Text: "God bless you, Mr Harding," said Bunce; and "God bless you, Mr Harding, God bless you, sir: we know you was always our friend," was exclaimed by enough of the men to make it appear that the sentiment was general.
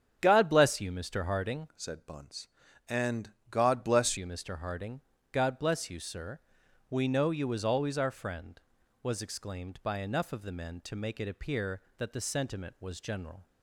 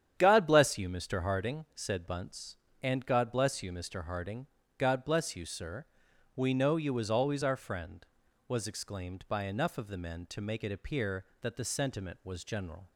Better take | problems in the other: second | starts louder than the rest; strong; until 1.2 s; 8 dB; strong in the second // changes voice from "said" to "bless"; from 1.7 to 4.1 s; 2.4 s long // pauses between "and" and "God"; slight; at 3.3 s; 0.16 s long

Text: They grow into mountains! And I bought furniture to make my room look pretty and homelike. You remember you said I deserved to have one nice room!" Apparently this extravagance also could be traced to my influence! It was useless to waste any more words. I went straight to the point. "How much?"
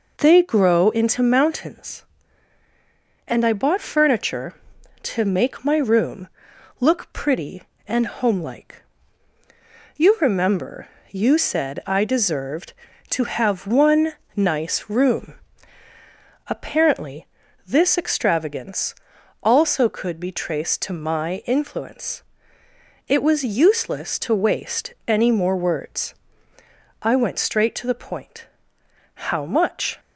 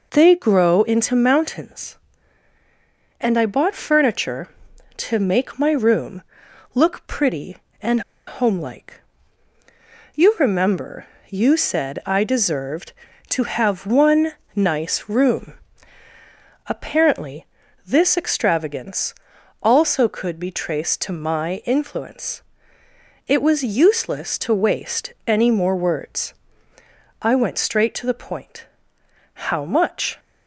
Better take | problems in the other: first | pauses between "room" and "look"; noticeable; at 6.2 s; 0.50 s long; noticeable in the first // pauses between "and" and "homelike"; slight; at 8.0 s; 0.26 s long // pauses between "remember" and "you"; slight; at 11.0 s; 0.24 s long; slight in the first // pauses between "one" and "nice"; slight; at 14.3 s; 0.22 s long; slight in the first // pauses between "Apparently" and "this"; at 17.4 s; 0.40 s long; also in the first // pauses between "extravagance" and "also"; noticeable; at 19.1 s; 0.48 s long; noticeable in the first

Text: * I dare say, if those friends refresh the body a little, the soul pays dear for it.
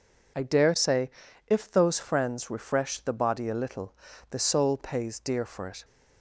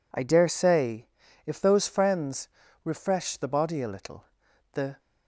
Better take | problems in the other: first | pauses between "friends" and "refresh"; slight; at 2.4 s; 0.36 s long // stops before "soul pays dear for it"; at 4.9 s

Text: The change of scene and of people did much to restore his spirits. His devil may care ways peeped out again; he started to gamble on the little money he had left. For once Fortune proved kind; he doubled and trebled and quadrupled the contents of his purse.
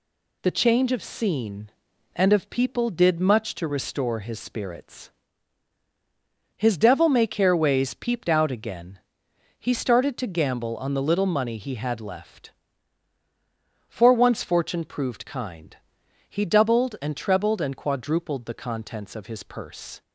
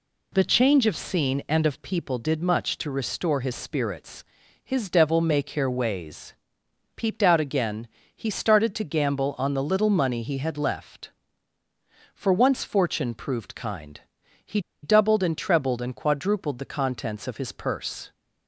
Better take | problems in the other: first | pauses between "ways" and "peeped"; noticeable; at 6.3 s; 0.62 s long // pauses between "he" and "doubled"; slight; at 14.5 s; 0.23 s long

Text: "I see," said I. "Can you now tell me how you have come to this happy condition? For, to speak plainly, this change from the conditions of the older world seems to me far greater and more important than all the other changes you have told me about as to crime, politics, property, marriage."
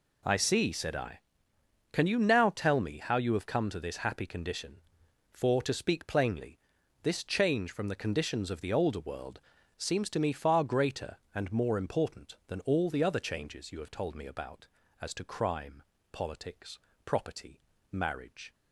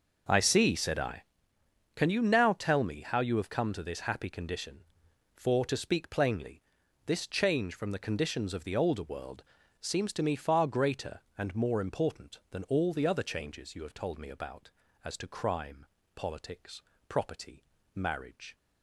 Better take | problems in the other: first | starts louder than the rest; noticeable; until 1.5 s; 6 dB // pauses between "world" and "seems"; slight; at 9.4 s; 0.36 s long; slight in the first

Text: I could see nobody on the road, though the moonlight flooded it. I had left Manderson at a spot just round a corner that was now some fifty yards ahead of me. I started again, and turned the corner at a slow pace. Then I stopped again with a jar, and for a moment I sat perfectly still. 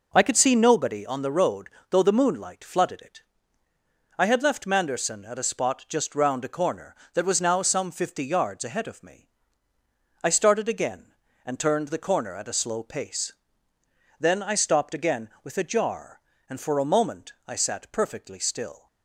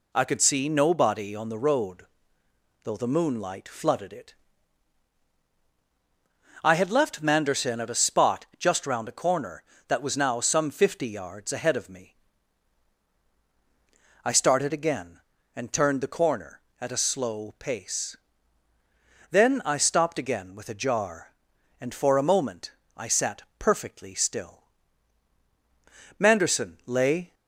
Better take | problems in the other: first | pauses between "moment" and "I"; slight; at 22.7 s; 0.24 s long // pauses between "sat" and "perfectly"; slight; at 23.4 s; 0.16 s long // goes on to say "Manderson lay"; noticeable; from 26.1 s on; 1.1 s long

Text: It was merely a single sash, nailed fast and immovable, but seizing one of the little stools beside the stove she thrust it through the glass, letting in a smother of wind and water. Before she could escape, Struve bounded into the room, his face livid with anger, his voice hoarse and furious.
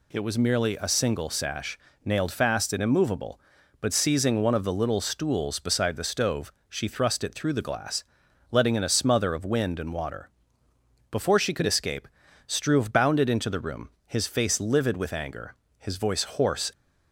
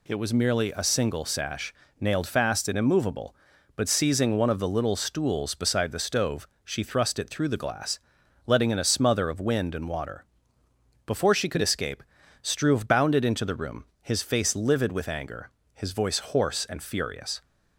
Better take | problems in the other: second | pauses between "stove" and "she"; slight; at 6.5 s; 0.16 s long; slight in the second // stops before "and furious"; at 16.7 s

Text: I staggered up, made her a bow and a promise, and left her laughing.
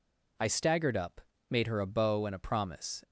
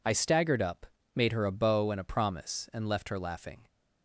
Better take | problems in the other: second | stops before "and left her laughing"; at 3.0 s

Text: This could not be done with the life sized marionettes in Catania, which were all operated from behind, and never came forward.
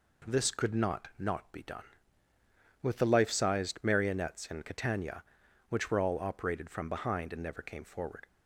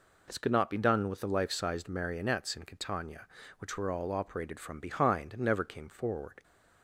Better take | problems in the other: second | says "not" twice; at 1.1 s

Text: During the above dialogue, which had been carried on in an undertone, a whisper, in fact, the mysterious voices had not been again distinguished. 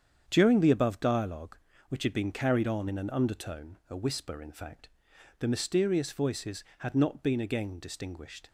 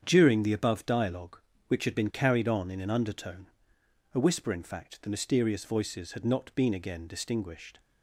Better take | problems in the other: neither | starts louder than the rest; strong; the same in both

